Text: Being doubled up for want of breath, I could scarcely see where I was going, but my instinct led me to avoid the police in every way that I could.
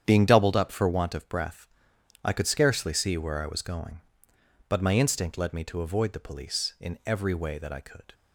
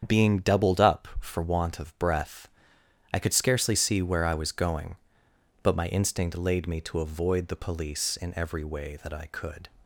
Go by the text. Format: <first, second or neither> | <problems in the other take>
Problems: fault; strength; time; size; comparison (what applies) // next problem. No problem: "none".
first | starts louder than the rest; strong; until 1.2 s; 8 dB; strong in the first // says "laid" for "led"; at 6.3 s